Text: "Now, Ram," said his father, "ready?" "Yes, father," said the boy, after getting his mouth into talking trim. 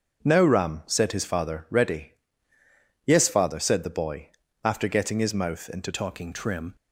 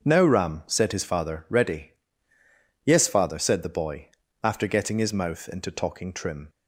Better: second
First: starts louder than the rest; until 1.2 s; 6.5 dB // changes voice at "talking"; from 5.9 s on; 0.8 s long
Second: starts louder than the rest; until 1.0 s; 6.5 dB

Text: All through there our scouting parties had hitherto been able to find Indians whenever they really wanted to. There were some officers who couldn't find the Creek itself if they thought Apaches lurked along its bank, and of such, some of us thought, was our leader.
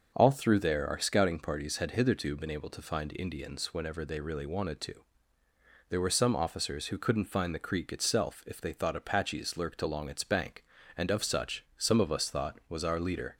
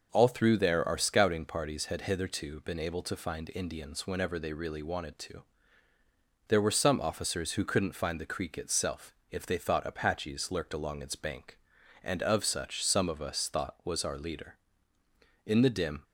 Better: first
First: none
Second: pauses between "itself" and "if"; slight; at 9.1 s; 0.16 s long // goes on to say "In the dim"; from 15.4 s on; 0.58 s long

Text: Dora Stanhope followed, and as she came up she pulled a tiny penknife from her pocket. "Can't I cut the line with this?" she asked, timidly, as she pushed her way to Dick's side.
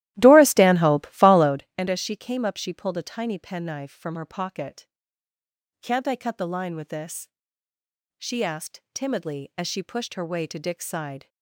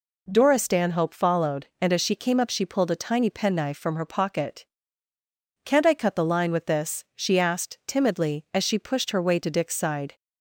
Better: second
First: starts louder than the rest; strong; until 1.7 s; 15 dB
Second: none

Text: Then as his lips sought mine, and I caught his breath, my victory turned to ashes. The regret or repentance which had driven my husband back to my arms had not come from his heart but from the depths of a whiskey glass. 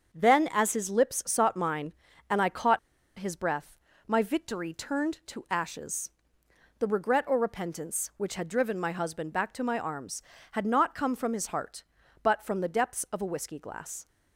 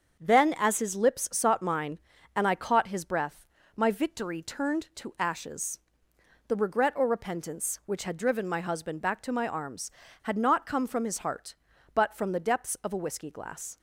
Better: second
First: starts louder than the rest; until 1.1 s; 7 dB // pauses between "caught" and "his"; at 2.7 s; 0.39 s long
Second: starts louder than the rest; until 1.2 s; 7 dB

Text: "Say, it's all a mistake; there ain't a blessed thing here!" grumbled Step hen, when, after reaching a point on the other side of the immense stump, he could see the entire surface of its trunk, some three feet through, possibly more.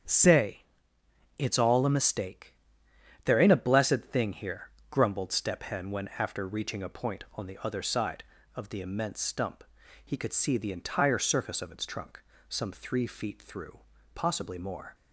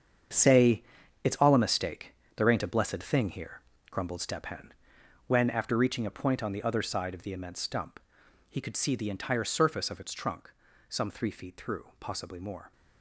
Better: first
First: starts louder than the rest; strong; until 1.8 s; 8 dB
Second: gets quieter; strong; throughout; 11 dB // starts louder than the rest; strong; until 1.8 s; 7.5 dB

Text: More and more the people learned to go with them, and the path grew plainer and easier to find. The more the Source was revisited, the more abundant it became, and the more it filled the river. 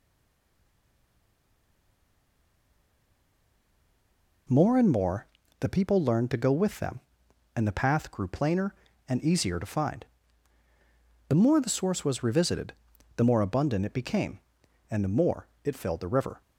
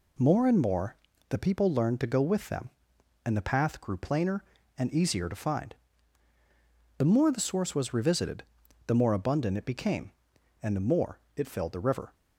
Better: second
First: stays silent before the first word; strong; until 4.4 s; 4.4 s long // pauses between "more" and "the"; slight; at 5.2 s; 0.32 s long // pauses between "more" and "it"; slight; at 15.4 s; 0.16 s long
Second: pauses between "more" and "the"; slight; at 0.9 s; 0.32 s long // pauses between "more" and "it"; slight; at 11.1 s; 0.16 s long

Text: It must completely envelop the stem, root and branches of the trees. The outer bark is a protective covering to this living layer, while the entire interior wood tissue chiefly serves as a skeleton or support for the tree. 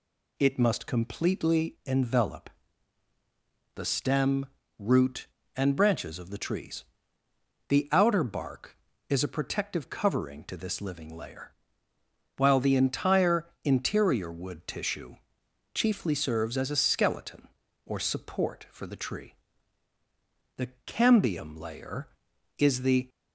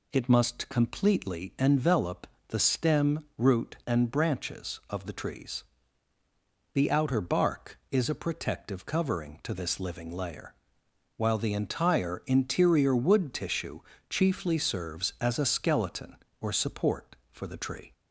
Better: second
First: pauses between "envelop" and "the"; strong; at 2.4 s; 1.2 s long // pauses between "entire" and "interior"; slight; at 13.4 s; 0.18 s long // pauses between "tissue" and "chiefly"; noticeable; at 15.1 s; 0.58 s long // goes on to say "The cambium layer is the"; strong; from 20.5 s on; 2.5 s long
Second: pauses between "envelop" and "the"; slight; at 2.2 s; 0.22 s long // pauses between "tissue" and "chiefly"; slight; at 13.8 s; 0.28 s long

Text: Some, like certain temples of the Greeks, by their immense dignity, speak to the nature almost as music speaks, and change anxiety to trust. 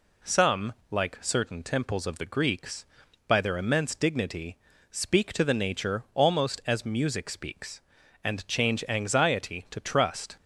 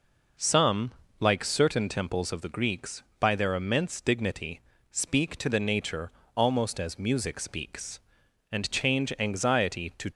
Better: first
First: none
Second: pauses between "nature" and "almost"; slight; at 6.1 s; 0.24 s long // stops before "trust"; at 10.1 s

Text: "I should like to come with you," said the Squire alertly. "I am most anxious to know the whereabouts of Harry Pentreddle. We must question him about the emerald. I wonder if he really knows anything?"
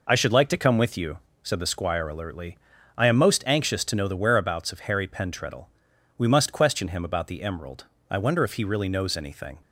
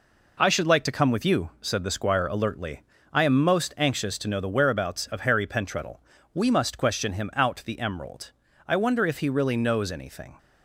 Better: first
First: none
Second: says "out" for "about"; at 7.3 s

